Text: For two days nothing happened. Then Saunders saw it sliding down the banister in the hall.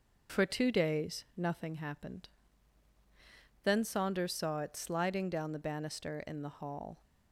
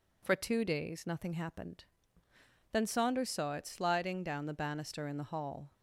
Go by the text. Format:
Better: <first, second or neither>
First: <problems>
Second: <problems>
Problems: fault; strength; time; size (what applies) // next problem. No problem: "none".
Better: neither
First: none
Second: none